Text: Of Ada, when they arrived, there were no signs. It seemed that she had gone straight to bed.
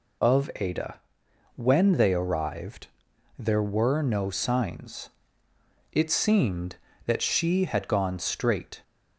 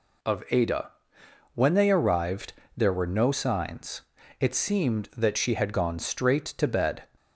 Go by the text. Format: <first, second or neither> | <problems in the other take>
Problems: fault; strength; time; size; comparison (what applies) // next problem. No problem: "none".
second | stops before "to bed"; at 8.8 s